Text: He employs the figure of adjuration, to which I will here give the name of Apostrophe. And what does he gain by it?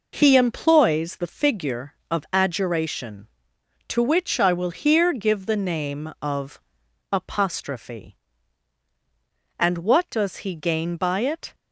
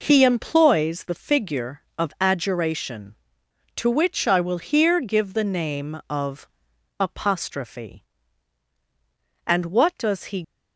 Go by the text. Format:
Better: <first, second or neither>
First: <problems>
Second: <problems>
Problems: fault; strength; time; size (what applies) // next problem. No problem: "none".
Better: first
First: pauses between "of" and "Apostrophe"; noticeable; at 6.6 s; 0.50 s long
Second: pauses between "of" and "Apostrophe"; noticeable; at 6.4 s; 0.50 s long // stops before "gain by it"; at 10.4 s